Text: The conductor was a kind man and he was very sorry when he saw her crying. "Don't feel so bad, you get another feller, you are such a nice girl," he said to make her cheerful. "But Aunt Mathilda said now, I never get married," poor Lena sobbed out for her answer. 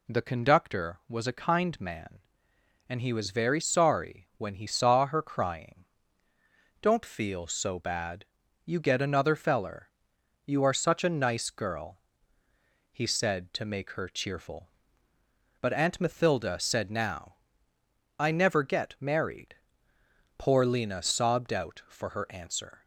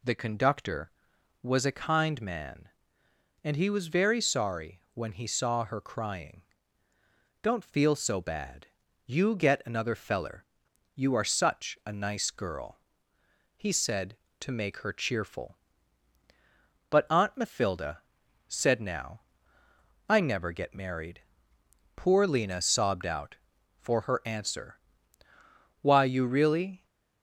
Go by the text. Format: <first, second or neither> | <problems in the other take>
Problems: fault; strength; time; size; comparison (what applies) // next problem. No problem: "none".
first | pauses between "Mathilda" and "said"; noticeable; at 18.0 s; 0.46 s long // goes on to say "Why you really"; noticeable; from 25.8 s on; 1.0 s long